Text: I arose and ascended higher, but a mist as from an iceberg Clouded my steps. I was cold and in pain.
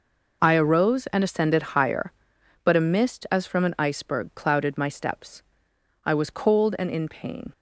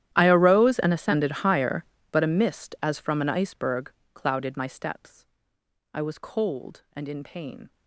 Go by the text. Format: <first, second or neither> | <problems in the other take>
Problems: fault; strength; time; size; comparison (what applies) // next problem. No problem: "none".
first | gets quieter; strong; throughout; 22.5 dB // pauses between "iceberg" and "Clouded"; slight; at 3.9 s; 0.22 s long